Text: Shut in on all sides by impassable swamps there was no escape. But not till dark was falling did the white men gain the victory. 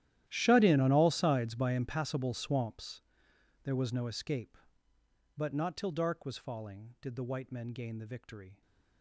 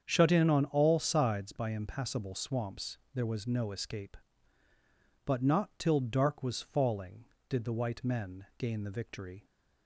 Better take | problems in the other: second | gets quieter; strong; throughout; 20.5 dB // starts louder than the rest; strong; until 1.2 s; 12.5 dB; strong in the second // pauses between "swamps" and "there"; noticeable; at 3.0 s; 0.62 s long; slight in the second

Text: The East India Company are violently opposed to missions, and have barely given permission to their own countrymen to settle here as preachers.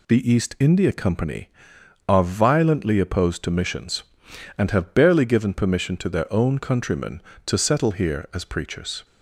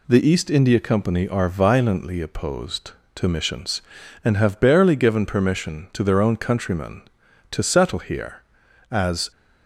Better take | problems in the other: first | stops before "preachers"; at 9.3 s

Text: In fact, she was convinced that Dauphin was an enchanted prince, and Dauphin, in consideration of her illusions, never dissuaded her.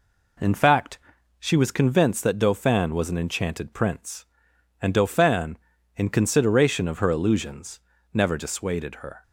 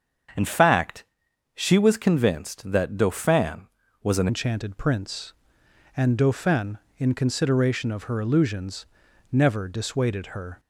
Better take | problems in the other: first | starts louder than the rest; strong; until 1.8 s; 7.5 dB // changes voice at "enchanted"; from 4.2 s on; 6.3 s long

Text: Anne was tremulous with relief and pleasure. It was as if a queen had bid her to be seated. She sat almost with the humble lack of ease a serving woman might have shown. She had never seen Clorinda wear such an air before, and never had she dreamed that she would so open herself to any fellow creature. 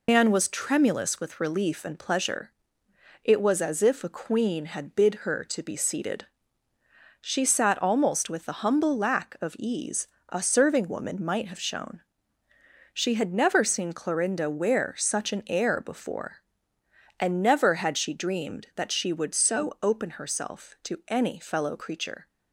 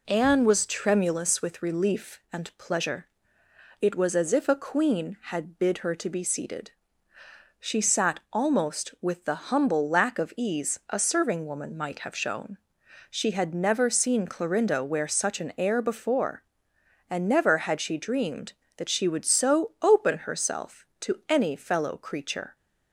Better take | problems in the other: second | loses the start of "Anne"; at 0.0 s; 40 ms // pauses between "ease" and "a"; slight; at 10.0 s; 0.20 s long

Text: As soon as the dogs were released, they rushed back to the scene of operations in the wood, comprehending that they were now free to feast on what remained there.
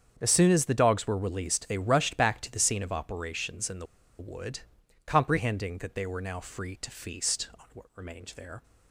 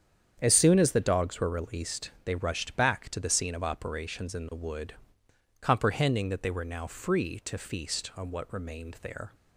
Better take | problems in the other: second | starts louder than the rest; strong; until 1.2 s; 7.5 dB; strong in the second // pauses between "the" and "wood"; slight; at 3.8 s; 0.33 s long

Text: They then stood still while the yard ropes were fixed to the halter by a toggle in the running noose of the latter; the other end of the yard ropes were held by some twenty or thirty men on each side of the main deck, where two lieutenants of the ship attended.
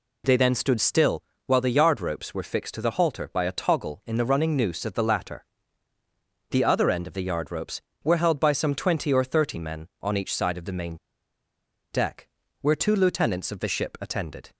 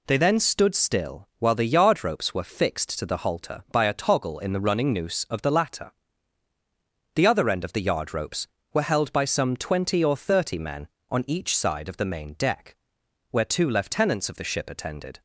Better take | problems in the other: second | pauses between "still" and "while"; slight; at 1.2 s; 0.24 s long // pauses between "main" and "deck"; noticeable; at 10.9 s; 0.96 s long

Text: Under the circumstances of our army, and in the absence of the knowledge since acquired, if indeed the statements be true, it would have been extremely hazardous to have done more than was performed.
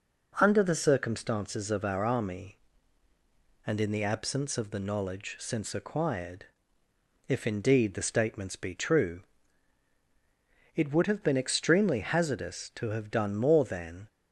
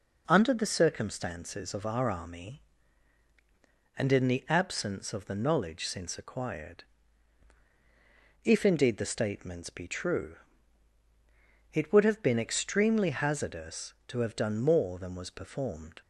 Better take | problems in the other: second | stops before "was performed"; at 14.0 s

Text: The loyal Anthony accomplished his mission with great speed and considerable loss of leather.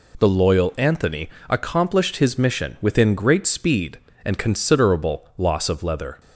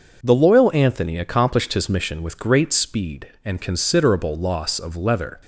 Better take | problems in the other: second | pauses between "Anthony" and "accomplished"; slight; at 1.2 s; 0.22 s long // says "within" for "with"; at 2.7 s

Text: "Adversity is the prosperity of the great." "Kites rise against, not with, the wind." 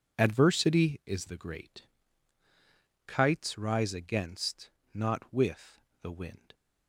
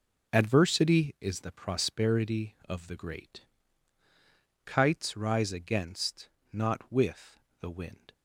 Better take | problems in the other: second | skips "the prosperity of"; at 1.2 s

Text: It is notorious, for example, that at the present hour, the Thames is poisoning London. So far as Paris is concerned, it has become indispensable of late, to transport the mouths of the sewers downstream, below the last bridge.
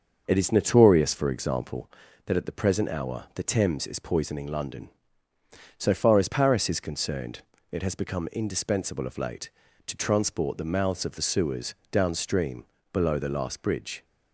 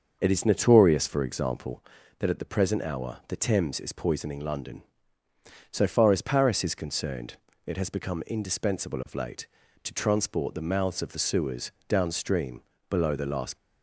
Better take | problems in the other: first | starts louder than the rest; until 1.2 s; 6 dB; also in the first // pauses between "sewers" and "downstream"; slight; at 11.7 s; 0.16 s long; slight in the first // stops before "bridge"; at 13.5 s

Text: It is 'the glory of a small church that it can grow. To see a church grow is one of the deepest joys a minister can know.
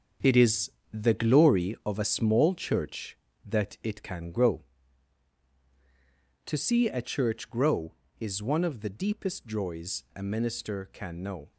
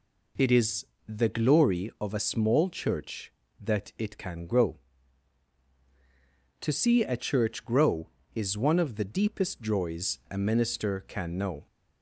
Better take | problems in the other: second | gets quieter; strong; throughout; 8.5 dB // pauses between "is" and "the"; slight; at 0.7 s; 0.22 s long; slight in the second

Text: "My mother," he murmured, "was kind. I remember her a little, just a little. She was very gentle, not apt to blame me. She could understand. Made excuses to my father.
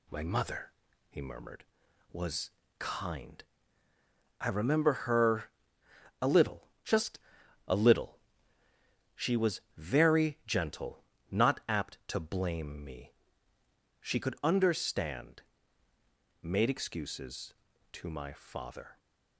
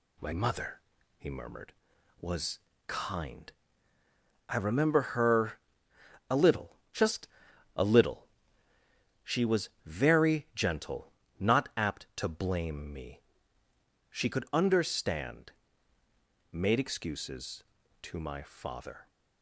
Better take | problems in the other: neither | pauses between "was" and "kind"; slight; the same in both // pauses between "her" and "a"; noticeable; the same in both // pauses between "just" and "a"; noticeable; the same in both // pauses between "was" and "very"; slight; the same in both

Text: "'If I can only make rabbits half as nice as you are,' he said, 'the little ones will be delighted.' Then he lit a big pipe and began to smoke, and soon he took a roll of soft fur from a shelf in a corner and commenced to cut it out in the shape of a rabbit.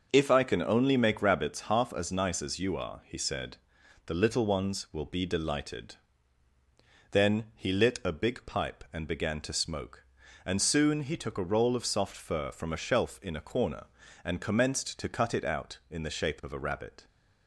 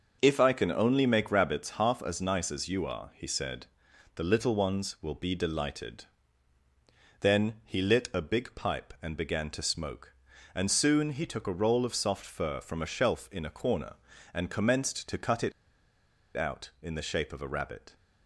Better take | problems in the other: first | starts louder than the rest; until 1.2 s; 6.5 dB; also in the first // pauses between "it" and "out"; noticeable; at 15.5 s; 0.83 s long

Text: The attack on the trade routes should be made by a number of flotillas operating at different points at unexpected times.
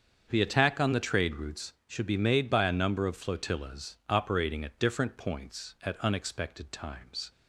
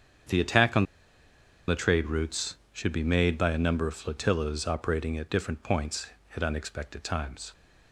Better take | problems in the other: first | starts louder than the rest; strong; until 2.1 s; 8 dB; strong in the first // pauses between "on" and "the"; noticeable; at 0.8 s; 0.84 s long

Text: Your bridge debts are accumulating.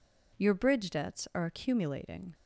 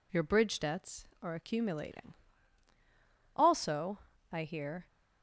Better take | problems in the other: first | goes on to say "Also I hear"; from 3.3 s on; 1.5 s long

